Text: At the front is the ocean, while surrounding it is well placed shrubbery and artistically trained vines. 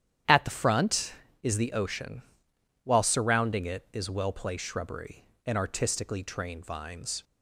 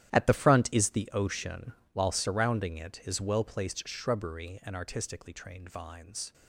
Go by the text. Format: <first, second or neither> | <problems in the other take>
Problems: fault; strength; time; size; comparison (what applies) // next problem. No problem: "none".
first | gets quieter; strong; throughout; 15 dB // starts louder than the rest; strong; until 1.1 s; 12 dB; strong in the first